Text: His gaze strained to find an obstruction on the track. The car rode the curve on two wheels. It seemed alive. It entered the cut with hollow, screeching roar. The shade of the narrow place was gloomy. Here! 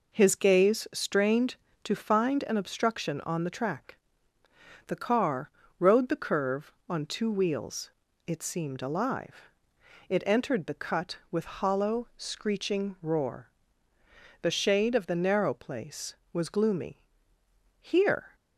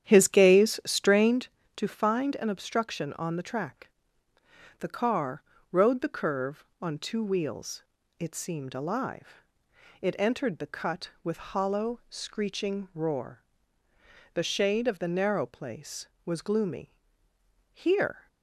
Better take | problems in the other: first | starts louder than the rest; strong; until 1.4 s; 9.5 dB // pauses between "car" and "rode"; slight; at 5.4 s; 0.30 s long; slight in the first

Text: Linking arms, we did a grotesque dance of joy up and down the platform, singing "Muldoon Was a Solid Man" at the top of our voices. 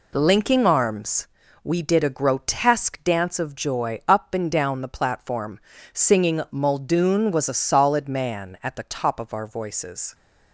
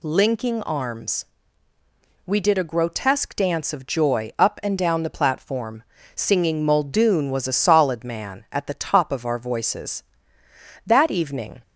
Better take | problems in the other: first | goes on to say "That evening"; noticeable; from 10.8 s on; 0.74 s long

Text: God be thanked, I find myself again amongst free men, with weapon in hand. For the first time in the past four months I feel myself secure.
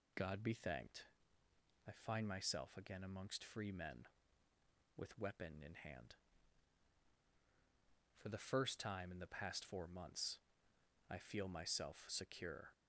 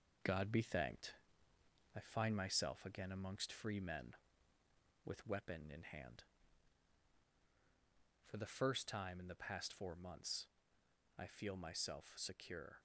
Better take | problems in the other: first | gets quieter; noticeable; throughout; 4 dB // pauses between "months" and "I"; noticeable; at 10.4 s; 0.70 s long; noticeable in the first

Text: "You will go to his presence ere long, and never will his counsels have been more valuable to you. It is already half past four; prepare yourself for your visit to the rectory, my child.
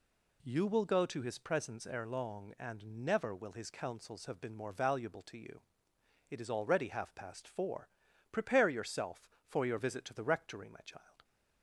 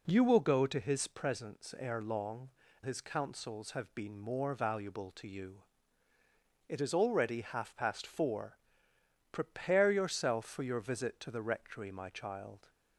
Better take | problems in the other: first | skips "and never will"; at 2.6 s

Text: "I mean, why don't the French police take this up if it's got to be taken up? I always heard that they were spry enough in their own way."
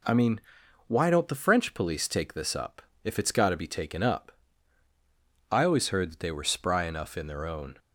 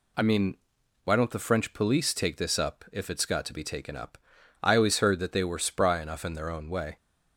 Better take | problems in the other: second | pauses between "up" and "if"; slight; at 2.8 s; 0.22 s long // stops before "way"; at 7.7 s

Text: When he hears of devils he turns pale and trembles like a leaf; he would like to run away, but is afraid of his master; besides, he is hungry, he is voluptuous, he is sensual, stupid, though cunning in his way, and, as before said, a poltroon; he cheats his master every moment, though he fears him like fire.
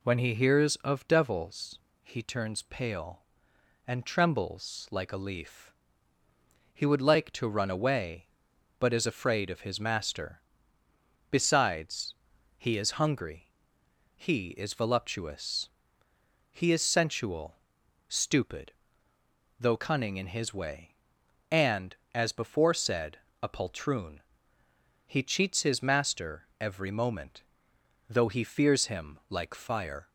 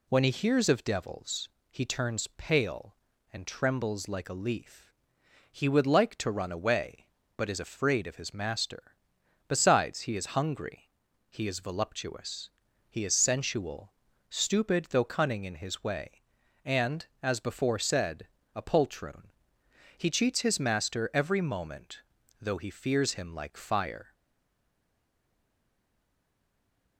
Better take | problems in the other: first | pauses between "devils" and "he"; slight; at 1.5 s; 0.20 s long; slight in the first // stays silent after the last word; strong; from 24.1 s on; 2.8 s long

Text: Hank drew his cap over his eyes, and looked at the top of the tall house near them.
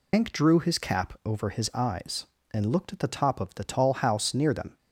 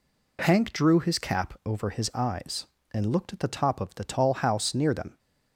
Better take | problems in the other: second | loses the start of "Hank"; at 0.1 s; 145 ms

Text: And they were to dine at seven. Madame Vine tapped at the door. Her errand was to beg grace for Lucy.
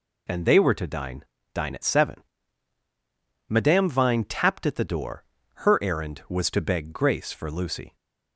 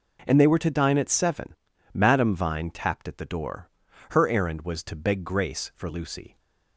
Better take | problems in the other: second | says "dine" twice; at 1.5 s

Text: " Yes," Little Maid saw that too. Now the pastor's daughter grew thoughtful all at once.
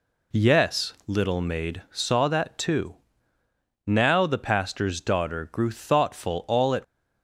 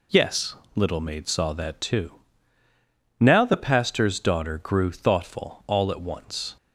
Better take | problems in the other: second | stops before "once"; at 6.8 s

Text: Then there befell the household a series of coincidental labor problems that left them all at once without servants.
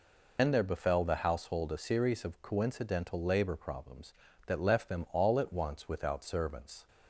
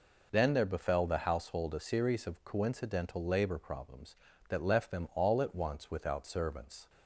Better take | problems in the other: second | loses the start of "Then"; at 0.3 s; 105 ms

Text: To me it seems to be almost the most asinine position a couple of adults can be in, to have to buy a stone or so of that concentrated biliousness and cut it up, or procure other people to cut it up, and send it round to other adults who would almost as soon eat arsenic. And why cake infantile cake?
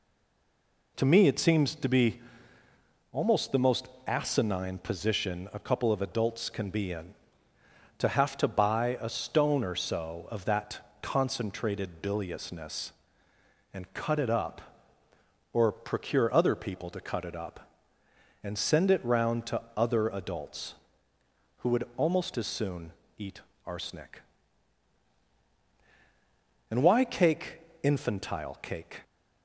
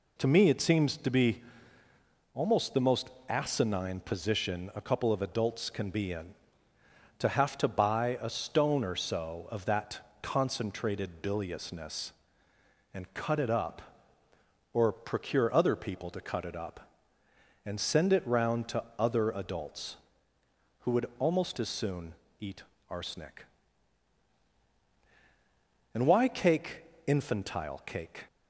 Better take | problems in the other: second | stays silent before the first word; slight; until 0.9 s; 0.9 s long // pauses between "be" and "almost"; noticeable; at 2.2 s; 0.92 s long; noticeable in the second // pauses between "most" and "asinine"; slight; at 3.8 s; 0.18 s long; slight in the second // pauses between "that" and "concentrated"; slight; at 10.7 s; 0.22 s long; slight in the second // pauses between "soon" and "eat"; slight; at 22.9 s; 0.24 s long; slight in the second // pauses between "eat" and "arsenic"; slight; at 23.4 s; 0.24 s long; slight in the second // pauses between "cake" and "infantile"; slight; at 27.6 s; 0.20 s long; slight in the second

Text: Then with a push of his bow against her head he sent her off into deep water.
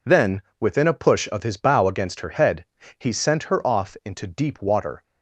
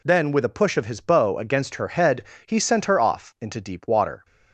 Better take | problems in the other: second | says "within" for "with"; at 0.6 s // pauses between "head" and "he"; slight; at 2.6 s; 0.32 s long; slight in the second

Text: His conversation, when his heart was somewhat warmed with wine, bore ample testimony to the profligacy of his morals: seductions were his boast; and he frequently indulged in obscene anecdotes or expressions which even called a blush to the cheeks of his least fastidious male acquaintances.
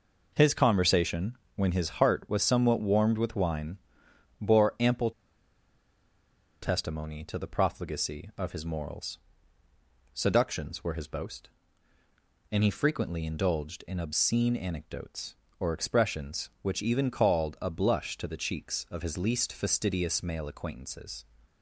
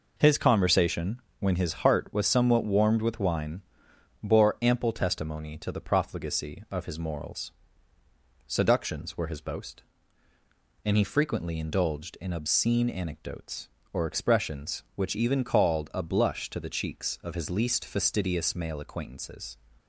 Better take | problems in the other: second | pauses between "ample" and "testimony"; strong; at 5.1 s; 1.5 s long

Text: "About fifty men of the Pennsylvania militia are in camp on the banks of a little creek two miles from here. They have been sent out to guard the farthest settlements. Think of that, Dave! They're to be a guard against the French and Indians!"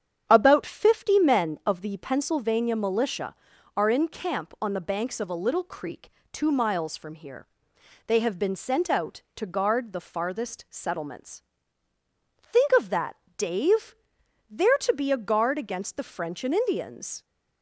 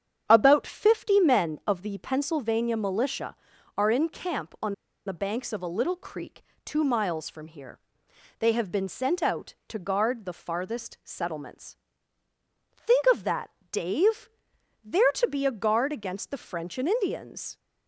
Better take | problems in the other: first | starts louder than the rest; strong; until 1.2 s; 8 dB; strong in the first // pauses between "on" and "the"; slight; at 4.7 s; 0.33 s long // pauses between "creek" and "two"; slight; at 6.4 s; 0.22 s long; slight in the first

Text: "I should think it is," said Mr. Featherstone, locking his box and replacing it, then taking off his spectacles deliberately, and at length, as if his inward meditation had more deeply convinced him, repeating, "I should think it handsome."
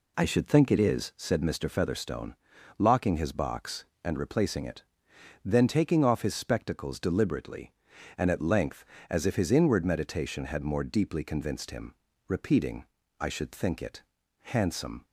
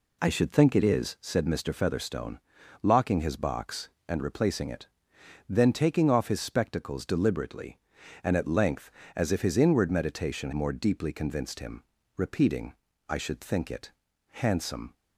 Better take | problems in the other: first | skips "had"; at 10.5 s // pauses between "it" and "handsome"; at 13.9 s; 0.38 s long; also in the first

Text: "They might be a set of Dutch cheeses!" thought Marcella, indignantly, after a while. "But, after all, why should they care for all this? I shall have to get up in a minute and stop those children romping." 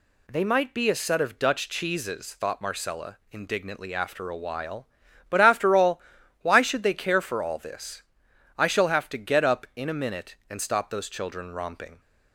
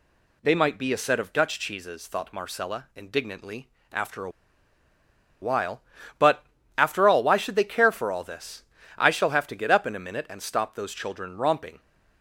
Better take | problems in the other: first | pauses between "a" and "while"; at 4.3 s; 1.1 s long

